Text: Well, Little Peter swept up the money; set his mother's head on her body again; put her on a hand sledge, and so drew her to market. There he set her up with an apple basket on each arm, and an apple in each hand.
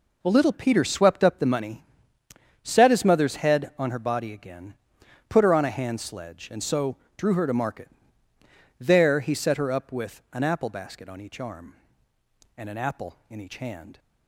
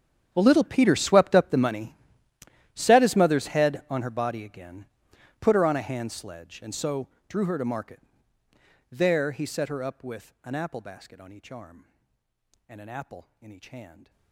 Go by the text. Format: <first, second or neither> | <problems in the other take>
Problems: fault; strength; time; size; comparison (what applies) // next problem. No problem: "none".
first | gets quieter; strong; throughout; 21 dB // pauses between "so" and "drew"; slight; at 7.0 s; 0.20 s long; slight in the first